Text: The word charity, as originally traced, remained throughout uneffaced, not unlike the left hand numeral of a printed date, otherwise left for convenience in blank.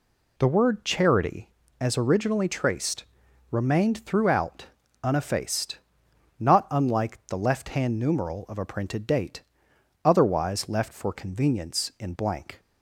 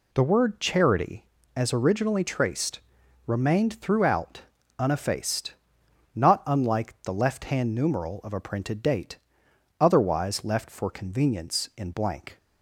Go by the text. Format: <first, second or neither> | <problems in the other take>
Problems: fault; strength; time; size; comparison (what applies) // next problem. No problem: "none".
neither | pauses between "throughout" and "uneffaced"; slight; the same in both